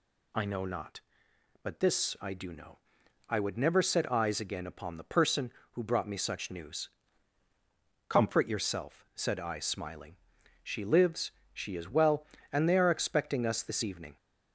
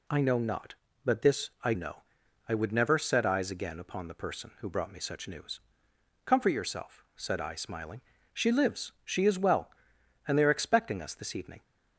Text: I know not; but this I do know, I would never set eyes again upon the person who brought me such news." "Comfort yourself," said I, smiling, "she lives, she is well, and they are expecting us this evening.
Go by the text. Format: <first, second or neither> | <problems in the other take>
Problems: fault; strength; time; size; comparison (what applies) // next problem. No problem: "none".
first | skips "do"; at 1.7 s